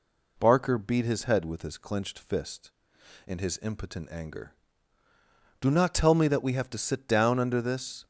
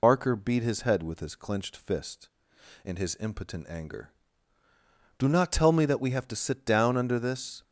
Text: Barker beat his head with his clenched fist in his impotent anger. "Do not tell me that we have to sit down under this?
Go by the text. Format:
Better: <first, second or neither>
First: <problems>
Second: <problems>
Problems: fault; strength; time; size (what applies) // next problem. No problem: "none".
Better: first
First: none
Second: loses the start of "Barker"; at 0.0 s; 80 ms